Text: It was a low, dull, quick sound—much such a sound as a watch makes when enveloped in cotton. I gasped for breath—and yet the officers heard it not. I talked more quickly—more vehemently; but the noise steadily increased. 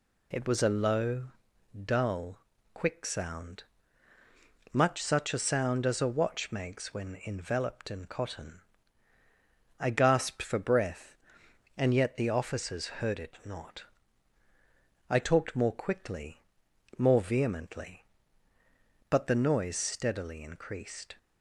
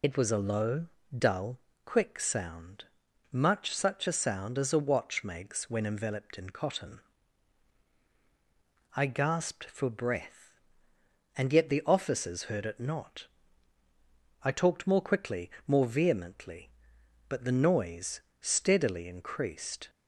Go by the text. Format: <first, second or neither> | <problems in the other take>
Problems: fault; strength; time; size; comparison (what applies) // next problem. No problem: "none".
first | loses the start of "It"; at 0.0 s; 30 ms // pauses between "noise" and "steadily"; slight; at 18.1 s; 0.20 s long